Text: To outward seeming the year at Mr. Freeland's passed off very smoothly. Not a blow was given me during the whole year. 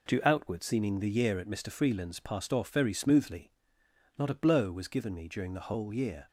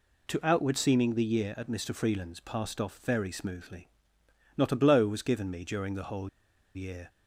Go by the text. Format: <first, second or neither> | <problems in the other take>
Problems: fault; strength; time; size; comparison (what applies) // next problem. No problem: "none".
first | pauses between "whole" and "year"; noticeable; at 6.2 s; 0.47 s long